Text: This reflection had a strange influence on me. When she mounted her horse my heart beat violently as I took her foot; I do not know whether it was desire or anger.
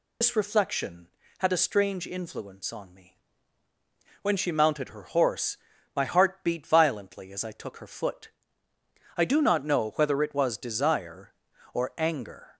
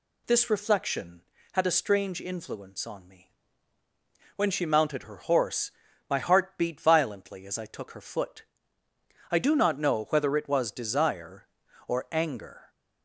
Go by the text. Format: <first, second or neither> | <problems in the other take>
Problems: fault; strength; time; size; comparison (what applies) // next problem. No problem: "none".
second | loses the start of "This"; at 0.2 s; 90 ms // pauses between "horse" and "my"; at 5.5 s; 0.38 s long; also in the second